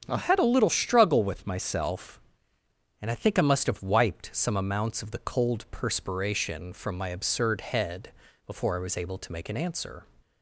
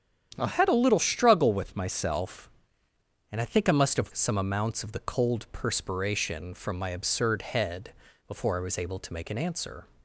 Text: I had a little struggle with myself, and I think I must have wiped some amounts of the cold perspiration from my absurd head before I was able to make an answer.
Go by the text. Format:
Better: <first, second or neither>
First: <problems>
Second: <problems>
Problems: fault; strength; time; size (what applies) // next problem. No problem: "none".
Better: first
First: starts louder than the rest; strong; until 1.0 s; 7.5 dB // pauses between "head" and "before"; slight; at 8.1 s; 0.34 s long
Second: starts louder than the rest; strong; until 1.3 s; 9 dB // skips "wiped"; at 4.1 s // pauses between "head" and "before"; slight; at 7.9 s; 0.34 s long